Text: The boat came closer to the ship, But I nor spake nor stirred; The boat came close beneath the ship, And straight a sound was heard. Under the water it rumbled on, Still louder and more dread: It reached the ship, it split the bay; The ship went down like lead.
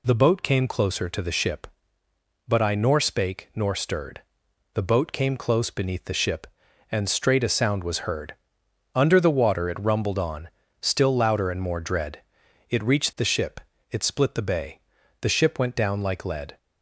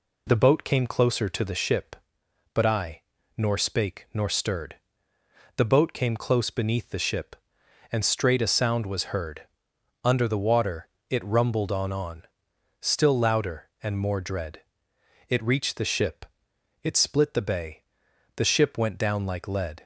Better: first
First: none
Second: pauses between "I" and "nor"; at 2.9 s; 0.38 s long // pauses between "water" and "it"; slight; at 10.8 s; 0.22 s long // says "on" twice; at 11.9 s

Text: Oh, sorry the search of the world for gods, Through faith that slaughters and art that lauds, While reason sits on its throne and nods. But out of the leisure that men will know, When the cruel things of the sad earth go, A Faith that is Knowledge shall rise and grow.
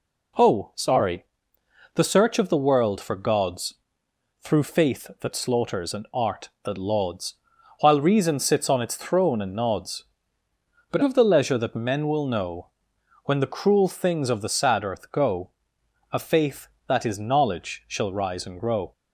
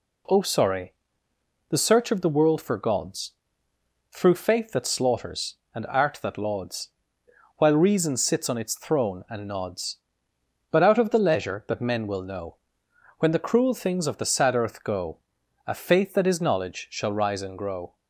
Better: second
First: pauses between "sorry" and "the"; noticeable; at 1.2 s; 0.70 s long // skips "out"; at 11.0 s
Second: pauses between "sorry" and "the"; noticeable; at 0.9 s; 0.76 s long

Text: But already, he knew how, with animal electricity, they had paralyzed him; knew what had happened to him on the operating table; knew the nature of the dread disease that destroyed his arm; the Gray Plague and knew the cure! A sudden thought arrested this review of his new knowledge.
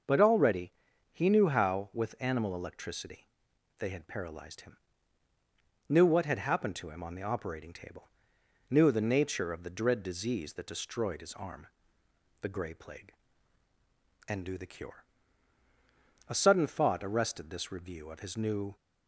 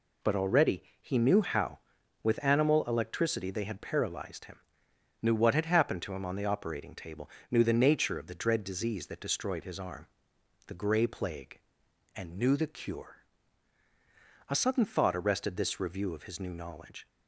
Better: second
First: starts louder than the rest; until 1.4 s; 6.5 dB // stops before "knowledge"; at 18.7 s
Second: none

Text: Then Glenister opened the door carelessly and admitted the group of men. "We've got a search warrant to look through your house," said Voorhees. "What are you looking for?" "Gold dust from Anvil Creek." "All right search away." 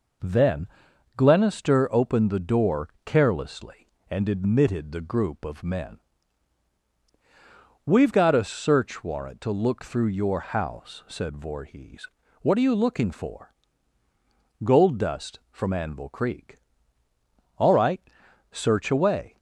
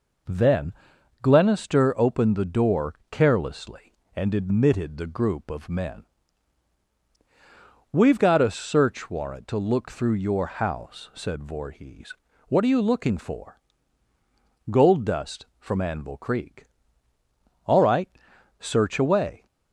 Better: neither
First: pauses between "Then" and "Glenister"; noticeable; at 0.6 s; 0.48 s long // pauses between "door" and "carelessly"; slight; at 2.8 s; 0.16 s long // pauses between "right" and "search"; noticeable; at 18.0 s; 0.50 s long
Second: pauses between "Then" and "Glenister"; noticeable; at 0.7 s; 0.48 s long // pauses between "door" and "carelessly"; slight; at 2.9 s; 0.16 s long // pauses between "right" and "search"; noticeable; at 18.0 s; 0.50 s long

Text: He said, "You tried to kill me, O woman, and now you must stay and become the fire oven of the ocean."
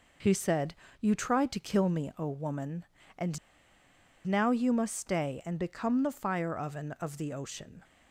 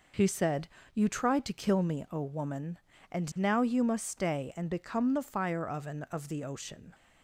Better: second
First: pauses between "and" and "now"; noticeable; at 3.3 s; 0.89 s long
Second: none

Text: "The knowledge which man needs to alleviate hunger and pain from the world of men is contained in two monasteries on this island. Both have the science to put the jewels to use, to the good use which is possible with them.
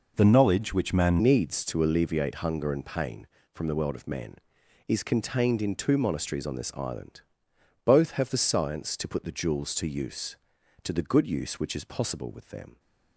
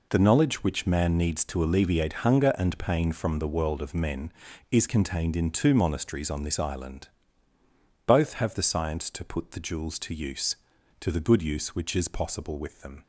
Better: second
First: changes voice at "needs"; from 1.2 s on; 11.5 s long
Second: none

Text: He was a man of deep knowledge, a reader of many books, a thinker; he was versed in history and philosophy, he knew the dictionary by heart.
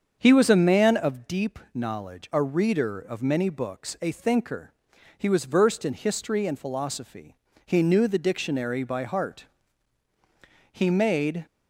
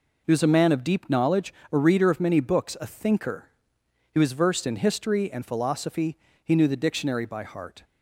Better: second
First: starts louder than the rest; strong; until 1.2 s; 7 dB // goes on to say "He made"; noticeable; from 10.7 s on; 0.74 s long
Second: none

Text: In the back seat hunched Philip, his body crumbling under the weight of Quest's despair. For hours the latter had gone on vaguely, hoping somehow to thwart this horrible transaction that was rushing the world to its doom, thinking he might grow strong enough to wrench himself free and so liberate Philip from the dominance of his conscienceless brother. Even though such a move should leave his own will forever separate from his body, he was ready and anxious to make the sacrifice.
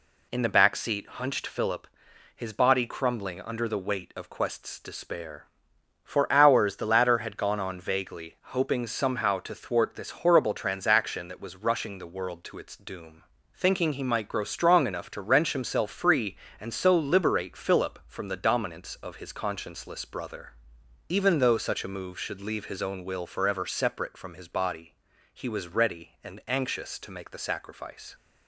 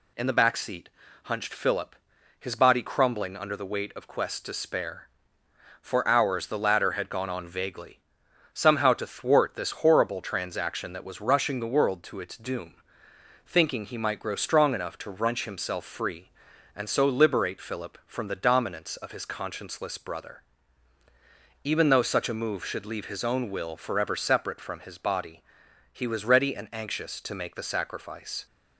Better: first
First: none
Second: pauses between "seat" and "hunched"; slight; at 0.8 s; 0.34 s long // skips "hoping"; at 8.2 s

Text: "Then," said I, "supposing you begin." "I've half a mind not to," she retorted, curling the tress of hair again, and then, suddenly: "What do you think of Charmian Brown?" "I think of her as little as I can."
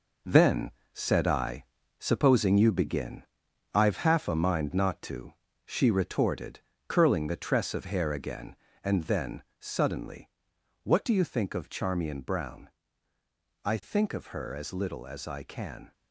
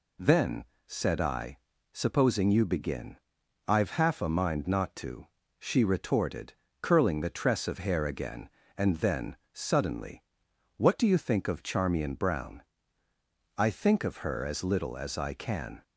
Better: second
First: gets quieter; strong; throughout; 8.5 dB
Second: none

